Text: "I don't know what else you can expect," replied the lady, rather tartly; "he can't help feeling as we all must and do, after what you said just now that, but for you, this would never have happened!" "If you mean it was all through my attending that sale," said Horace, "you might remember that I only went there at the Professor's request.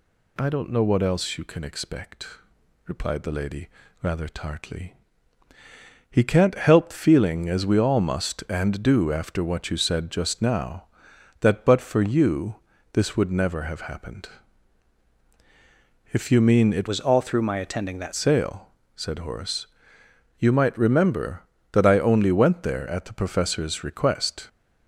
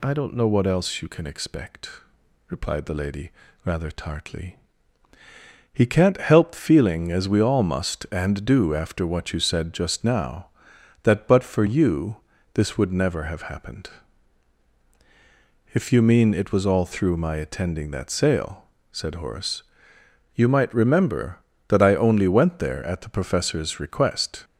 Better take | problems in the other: second | changes voice from "was" to "that"; from 16.8 to 18.1 s; 1.3 s long

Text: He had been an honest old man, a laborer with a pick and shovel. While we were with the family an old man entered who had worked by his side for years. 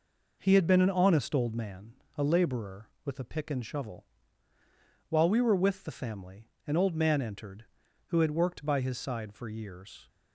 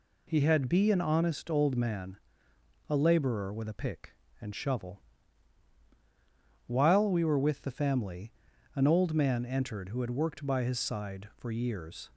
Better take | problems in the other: first | says "be" for "been"; at 0.6 s // pauses between "family" and "an"; at 8.3 s; 0.42 s long; slight in the first

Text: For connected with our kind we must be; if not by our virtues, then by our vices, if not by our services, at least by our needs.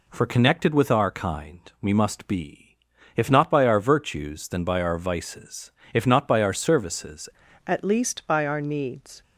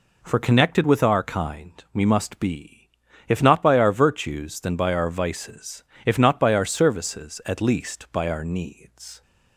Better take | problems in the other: second | changes voice at "at"; from 7.6 s on; 1.6 s long

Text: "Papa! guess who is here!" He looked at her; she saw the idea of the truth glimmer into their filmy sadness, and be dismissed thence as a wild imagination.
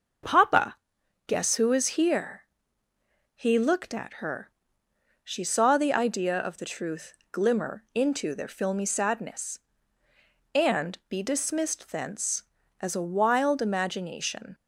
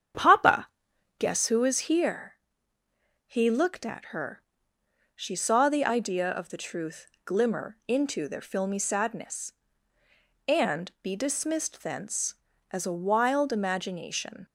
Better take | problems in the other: first | starts louder than the rest; strong; until 1.3 s; 8 dB // pauses between "truth" and "glimmer"; slight; at 7.0 s; 0.20 s long; slight in the first

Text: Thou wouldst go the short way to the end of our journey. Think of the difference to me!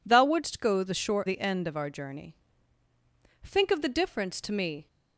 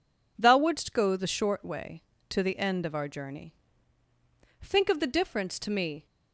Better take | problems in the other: second | skips "way to"; at 1.2 s

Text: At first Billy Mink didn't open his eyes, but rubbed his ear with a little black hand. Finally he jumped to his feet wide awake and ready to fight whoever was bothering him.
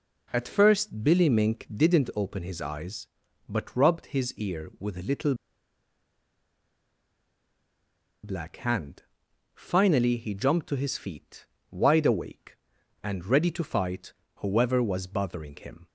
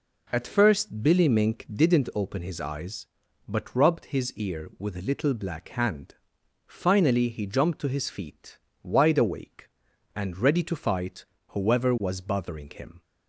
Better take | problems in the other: second | pauses between "little" and "black"; strong; at 5.3 s; 2.8 s long // pauses between "feet" and "wide"; slight; at 11.4 s; 0.26 s long; slight in the second // pauses between "fight" and "whoever"; slight; at 14.1 s; 0.24 s long; slight in the second

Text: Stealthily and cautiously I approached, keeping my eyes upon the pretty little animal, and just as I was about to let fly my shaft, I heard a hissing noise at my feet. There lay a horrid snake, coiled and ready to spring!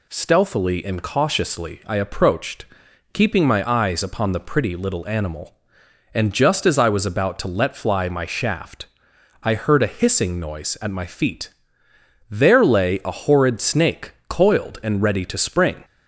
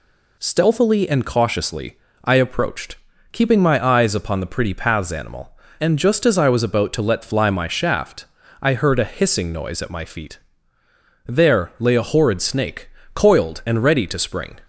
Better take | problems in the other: first | pauses between "cautiously" and "I"; slight; at 1.9 s; 0.26 s long // says "paths" for "little"; at 4.7 s

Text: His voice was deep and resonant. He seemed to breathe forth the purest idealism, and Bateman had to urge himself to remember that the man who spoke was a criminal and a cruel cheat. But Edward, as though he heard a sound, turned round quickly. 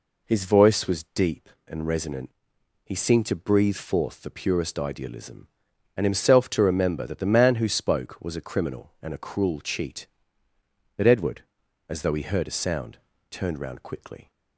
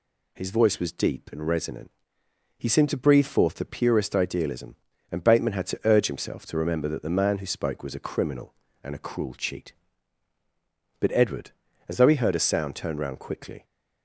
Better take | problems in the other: second | skips "Bateman had to urge"; at 6.0 s

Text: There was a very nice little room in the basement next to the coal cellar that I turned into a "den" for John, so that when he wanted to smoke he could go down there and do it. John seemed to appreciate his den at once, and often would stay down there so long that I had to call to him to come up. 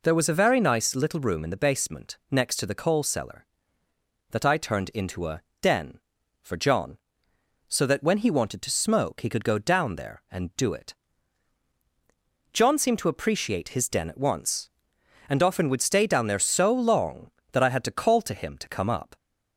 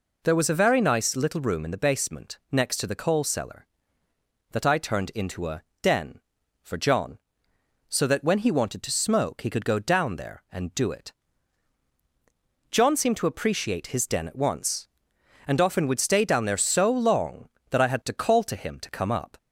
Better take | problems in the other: neither | pauses between "a" and "den"; slight; the same in both

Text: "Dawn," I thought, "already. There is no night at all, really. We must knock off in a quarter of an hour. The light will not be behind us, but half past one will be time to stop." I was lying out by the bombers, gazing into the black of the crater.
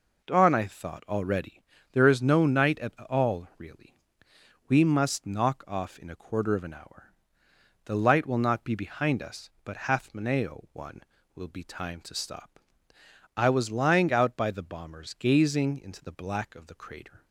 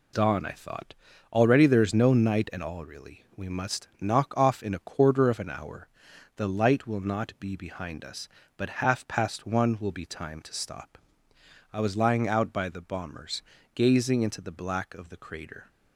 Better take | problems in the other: second | says "maneo" for "past"; at 10.1 s

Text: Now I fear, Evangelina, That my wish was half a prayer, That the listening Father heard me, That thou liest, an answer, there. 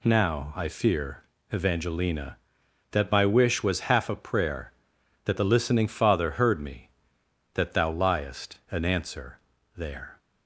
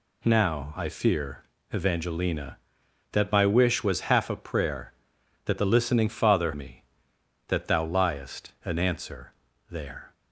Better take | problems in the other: first | skips "heard"; at 6.5 s

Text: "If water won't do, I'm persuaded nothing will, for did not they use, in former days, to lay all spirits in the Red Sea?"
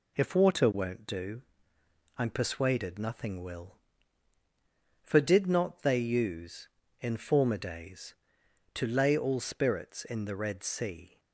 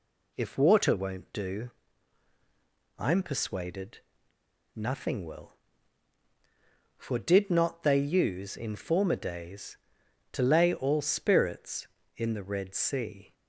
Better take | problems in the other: first | pauses between "persuaded" and "nothing"; noticeable; at 3.9 s; 0.76 s long

